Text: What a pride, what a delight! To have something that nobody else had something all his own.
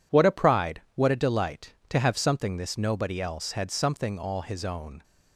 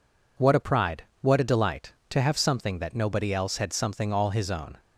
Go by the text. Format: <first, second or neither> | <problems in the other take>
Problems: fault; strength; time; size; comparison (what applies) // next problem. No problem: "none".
second | says "this" for "that"; at 2.5 s